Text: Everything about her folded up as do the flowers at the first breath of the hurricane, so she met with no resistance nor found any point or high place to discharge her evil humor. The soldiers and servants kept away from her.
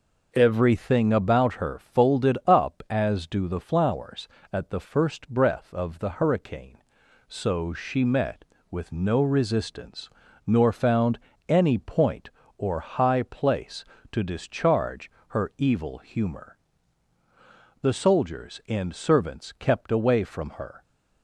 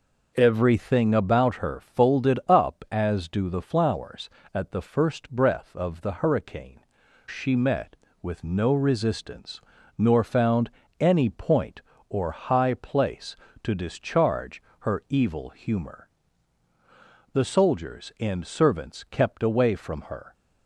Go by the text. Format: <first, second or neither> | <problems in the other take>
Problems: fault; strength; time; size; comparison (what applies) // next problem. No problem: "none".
first | skips "so"; at 7.0 s // pauses between "resistance" and "nor"; at 9.5 s; 0.38 s long; also in the first // pauses between "found" and "any"; slight; at 10.6 s; 0.32 s long; slight in the first // pauses between "discharge" and "her"; slight; at 14.6 s; 0.16 s long; slight in the first